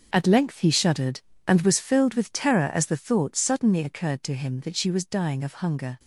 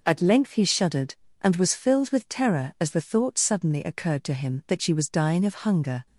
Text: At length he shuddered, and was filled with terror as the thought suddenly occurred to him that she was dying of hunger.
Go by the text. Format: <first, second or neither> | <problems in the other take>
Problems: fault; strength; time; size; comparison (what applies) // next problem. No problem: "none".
second | gets quieter; strong; throughout; 12 dB